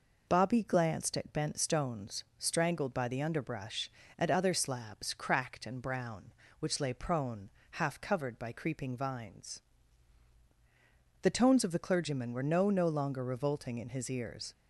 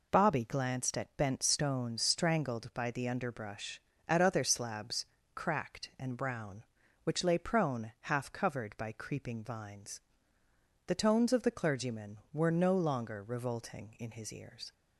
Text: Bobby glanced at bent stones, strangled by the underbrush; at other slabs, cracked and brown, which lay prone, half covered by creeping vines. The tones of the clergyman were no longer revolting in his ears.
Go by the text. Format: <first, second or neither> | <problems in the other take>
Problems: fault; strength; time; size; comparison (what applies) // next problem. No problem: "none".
second | says "no" twice; at 12.6 s